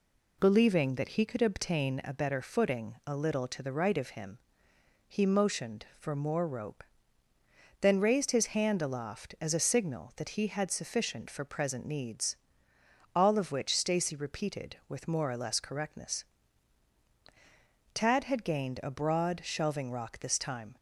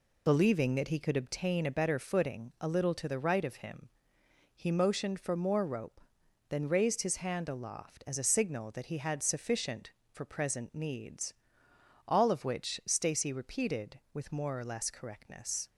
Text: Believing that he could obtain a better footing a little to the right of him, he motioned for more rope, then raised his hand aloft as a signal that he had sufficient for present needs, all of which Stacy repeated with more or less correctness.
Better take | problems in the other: second | goes on to say "Tad had gained a broad shelving rock this time"; strong; from 17.9 s on; 2.8 s long

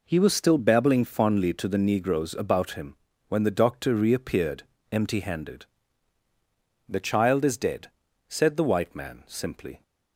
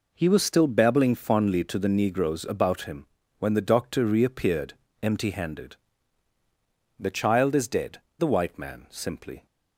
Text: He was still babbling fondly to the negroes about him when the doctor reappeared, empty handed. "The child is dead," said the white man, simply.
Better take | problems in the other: first | pauses between "him" and "when"; slight; at 3.0 s; 0.32 s long; slight in the first // skips "said"; at 8.0 s

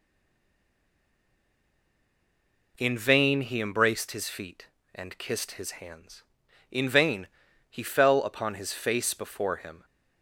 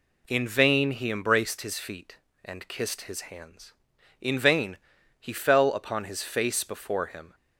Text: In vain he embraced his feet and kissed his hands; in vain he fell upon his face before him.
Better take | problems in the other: second | stays silent before the first word; strong; until 2.7 s; 2.7 s long // pauses between "vain" and "he"; at 7.2 s; 0.42 s long; also in the second

